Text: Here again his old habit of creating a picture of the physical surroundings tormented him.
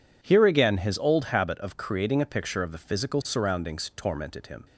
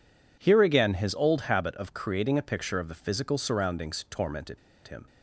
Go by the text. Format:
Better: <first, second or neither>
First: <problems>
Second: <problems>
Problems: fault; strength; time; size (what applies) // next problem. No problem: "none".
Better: first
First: none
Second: pauses between "tormented" and "him"; slight; at 4.5 s; 0.28 s long